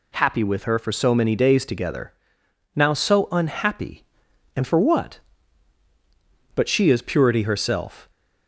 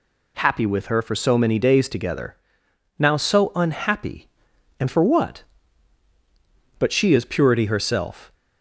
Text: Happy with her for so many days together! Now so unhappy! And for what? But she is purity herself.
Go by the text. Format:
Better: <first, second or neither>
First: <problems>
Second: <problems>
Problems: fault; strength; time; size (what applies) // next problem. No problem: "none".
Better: neither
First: none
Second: none